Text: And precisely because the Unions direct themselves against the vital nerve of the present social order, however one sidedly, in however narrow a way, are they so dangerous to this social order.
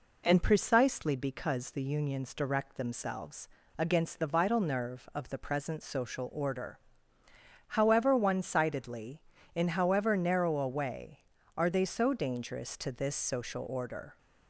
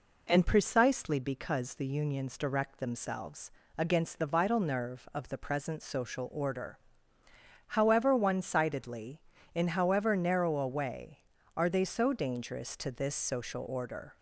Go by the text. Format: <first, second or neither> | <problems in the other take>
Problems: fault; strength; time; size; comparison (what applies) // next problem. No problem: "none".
neither | pauses between "themselves" and "against"; slight; the same in both